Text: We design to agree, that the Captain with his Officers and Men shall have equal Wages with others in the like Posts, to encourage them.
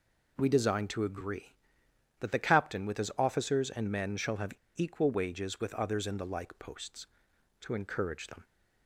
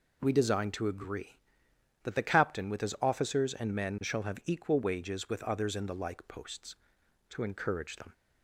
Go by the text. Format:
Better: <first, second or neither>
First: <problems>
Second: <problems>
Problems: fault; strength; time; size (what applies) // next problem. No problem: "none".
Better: second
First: pauses between "have" and "equal"; slight; at 4.5 s; 0.23 s long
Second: none